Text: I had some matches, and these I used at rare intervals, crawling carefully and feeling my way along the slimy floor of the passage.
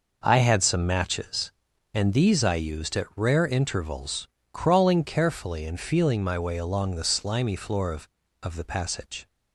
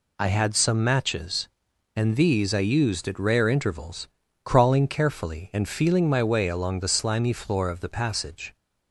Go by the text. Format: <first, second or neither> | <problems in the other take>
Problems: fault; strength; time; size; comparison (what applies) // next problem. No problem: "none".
second | says "of" twice; at 8.4 s